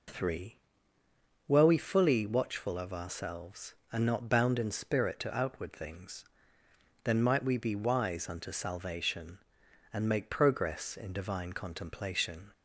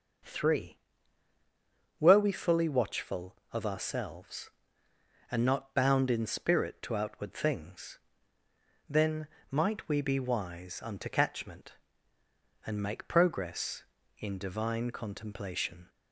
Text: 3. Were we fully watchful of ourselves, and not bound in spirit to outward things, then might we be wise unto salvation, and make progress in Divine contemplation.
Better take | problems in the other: first | pauses between "then" and "might"; slight; at 9.2 s; 0.22 s long // says "catchment" for "salvation"; at 11.0 s

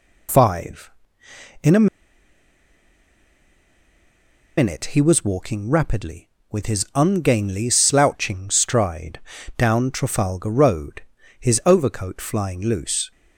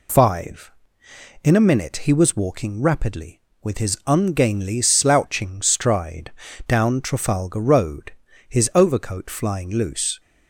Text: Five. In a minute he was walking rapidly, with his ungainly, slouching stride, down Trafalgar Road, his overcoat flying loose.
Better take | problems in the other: second | pauses between "a" and "minute"; strong; at 1.8 s; 2.7 s long

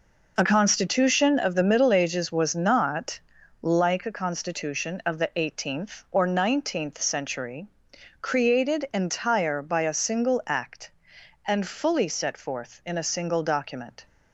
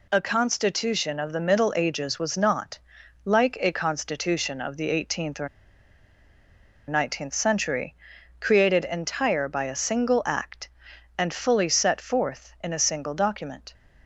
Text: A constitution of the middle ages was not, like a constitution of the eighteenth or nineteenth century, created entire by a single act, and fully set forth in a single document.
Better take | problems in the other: first | pauses between "or" and "nineteenth"; strong; at 5.4 s; 1.4 s long

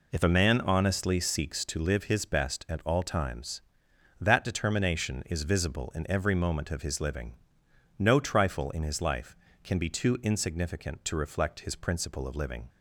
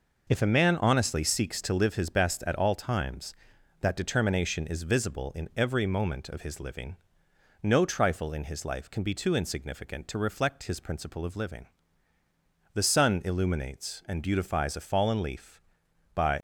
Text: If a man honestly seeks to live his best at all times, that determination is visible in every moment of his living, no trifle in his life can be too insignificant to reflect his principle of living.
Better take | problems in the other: first | goes on to say "The sun illuminates and beautifies a fallen leaf by"; strong; from 12.7 s on; 3.6 s long

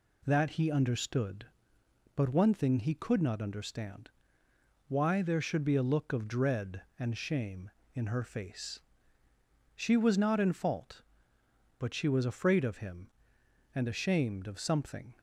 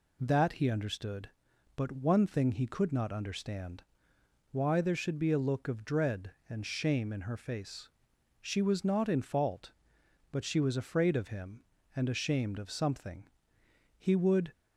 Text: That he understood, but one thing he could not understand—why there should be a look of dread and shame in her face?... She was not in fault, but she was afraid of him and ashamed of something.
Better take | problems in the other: first | goes on to say "He would"; from 13.9 s on; 0.54 s long

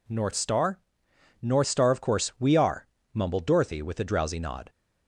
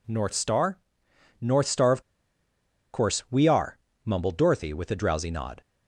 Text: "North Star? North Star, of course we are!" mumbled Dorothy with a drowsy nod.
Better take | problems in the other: first | pauses between "of" and "course"; noticeable; at 2.0 s; 0.90 s long

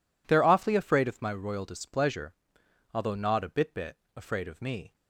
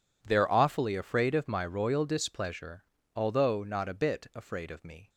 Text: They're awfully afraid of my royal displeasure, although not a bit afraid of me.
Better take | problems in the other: second | says "bit" twice; at 3.7 s

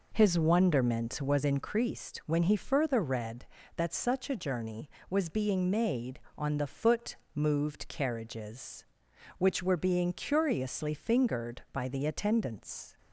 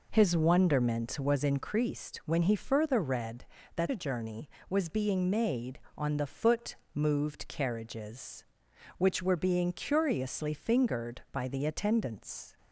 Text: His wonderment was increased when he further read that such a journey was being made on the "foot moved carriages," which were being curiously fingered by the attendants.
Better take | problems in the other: first | skips "such"; at 3.8 s // pauses between "foot" and "moved"; slight; at 6.7 s; 0.18 s long; slight in the first

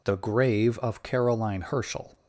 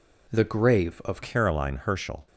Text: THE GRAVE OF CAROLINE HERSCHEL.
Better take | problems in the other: first | changes voice at "CAROLINE"; from 1.2 s on; 1.0 s long

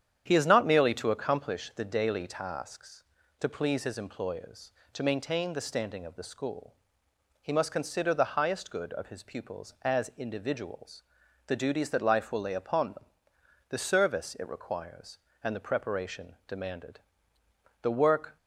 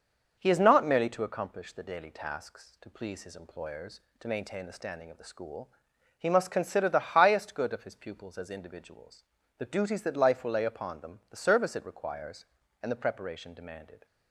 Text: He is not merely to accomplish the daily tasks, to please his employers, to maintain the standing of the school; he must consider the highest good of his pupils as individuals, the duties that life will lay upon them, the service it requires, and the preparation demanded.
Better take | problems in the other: second | starts louder than the rest; strong; until 1.2 s; 9 dB // pauses between "preparation" and "demanded"; slight; at 16.3 s; 0.16 s long // goes on to say "The work"; from 17.8 s on; 0.54 s long

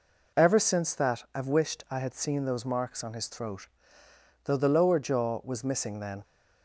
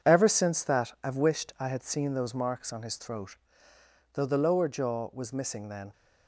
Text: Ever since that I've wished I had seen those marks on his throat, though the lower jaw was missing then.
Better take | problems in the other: first | gets quieter; throughout; 7 dB

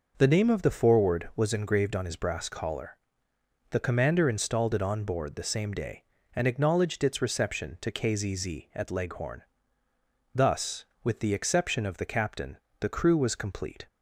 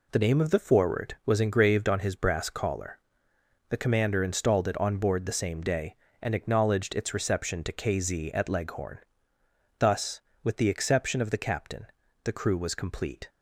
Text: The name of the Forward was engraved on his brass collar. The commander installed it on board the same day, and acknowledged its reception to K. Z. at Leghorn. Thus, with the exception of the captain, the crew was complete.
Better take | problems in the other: second | says "Z" twice; at 8.3 s

